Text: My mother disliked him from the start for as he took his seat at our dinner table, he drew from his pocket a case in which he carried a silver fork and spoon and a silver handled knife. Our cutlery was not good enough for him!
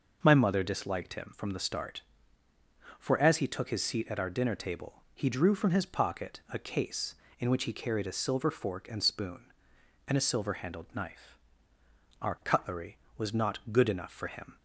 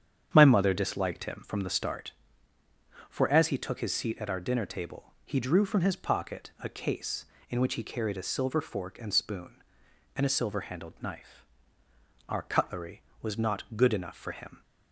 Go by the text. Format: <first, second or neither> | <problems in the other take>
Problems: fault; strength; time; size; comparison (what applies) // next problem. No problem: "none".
first | starts louder than the rest; strong; until 2.0 s; 8.5 dB